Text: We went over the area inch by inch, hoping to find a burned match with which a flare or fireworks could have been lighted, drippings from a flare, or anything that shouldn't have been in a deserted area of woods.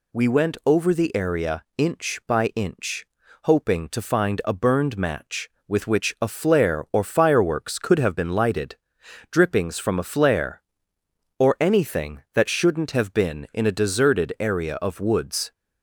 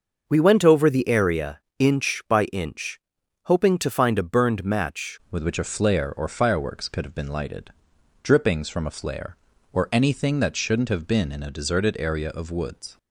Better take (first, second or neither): first